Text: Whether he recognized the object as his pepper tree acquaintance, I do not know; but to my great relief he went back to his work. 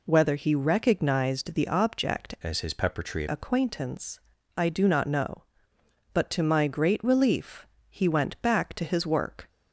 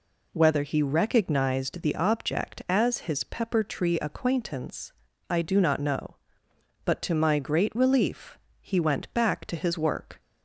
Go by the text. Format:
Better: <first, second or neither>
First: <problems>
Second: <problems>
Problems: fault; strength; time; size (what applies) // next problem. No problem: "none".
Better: second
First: changes voice from "as" to "tree"; from 2.4 to 3.2 s; 0.8 s long // pauses between "relief" and "he"; slight; at 7.6 s; 0.24 s long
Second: pauses between "relief" and "he"; slight; at 8.3 s; 0.24 s long